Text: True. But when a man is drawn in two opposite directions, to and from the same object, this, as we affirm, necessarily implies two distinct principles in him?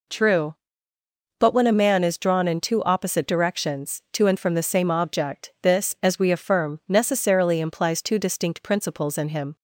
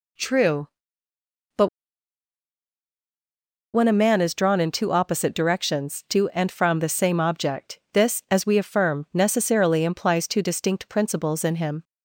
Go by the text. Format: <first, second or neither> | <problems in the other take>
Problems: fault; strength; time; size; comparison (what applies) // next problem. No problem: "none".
first | pauses between "But" and "when"; strong; at 1.6 s; 2.0 s long